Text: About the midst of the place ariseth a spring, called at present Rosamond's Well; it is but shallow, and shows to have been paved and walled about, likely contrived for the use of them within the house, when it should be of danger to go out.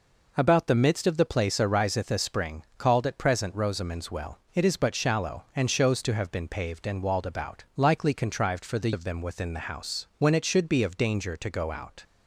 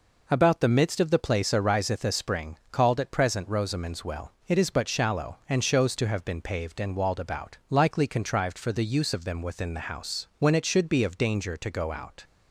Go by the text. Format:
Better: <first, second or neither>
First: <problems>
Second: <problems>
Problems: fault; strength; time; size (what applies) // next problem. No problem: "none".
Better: second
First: skips "use"; at 8.9 s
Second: none